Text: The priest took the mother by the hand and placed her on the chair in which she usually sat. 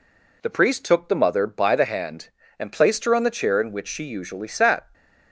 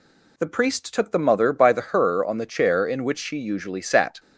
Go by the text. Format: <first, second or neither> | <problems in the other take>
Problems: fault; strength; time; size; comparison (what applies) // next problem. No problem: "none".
first | skips "hand and placed"; at 1.7 s